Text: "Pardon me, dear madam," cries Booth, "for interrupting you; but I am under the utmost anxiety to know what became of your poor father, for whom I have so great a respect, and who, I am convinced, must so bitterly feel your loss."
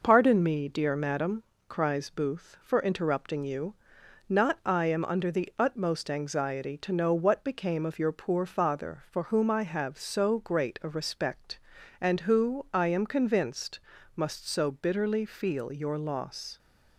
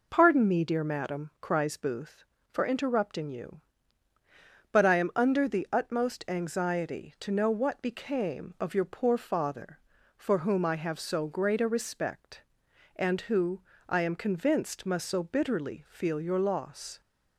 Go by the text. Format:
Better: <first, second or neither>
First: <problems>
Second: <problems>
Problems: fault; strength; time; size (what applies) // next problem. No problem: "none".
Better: second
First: says "not" for "but"; at 4.2 s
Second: none